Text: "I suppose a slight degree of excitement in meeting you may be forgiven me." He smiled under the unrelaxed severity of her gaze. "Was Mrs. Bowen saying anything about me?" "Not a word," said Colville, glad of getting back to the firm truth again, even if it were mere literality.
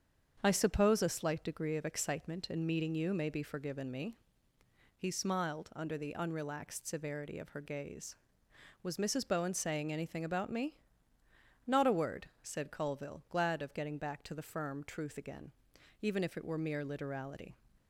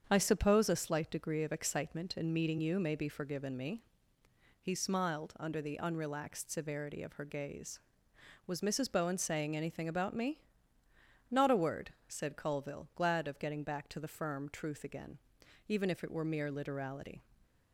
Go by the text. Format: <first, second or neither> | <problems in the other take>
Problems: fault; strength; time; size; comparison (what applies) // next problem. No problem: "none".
neither | starts louder than the rest; strong; the same in both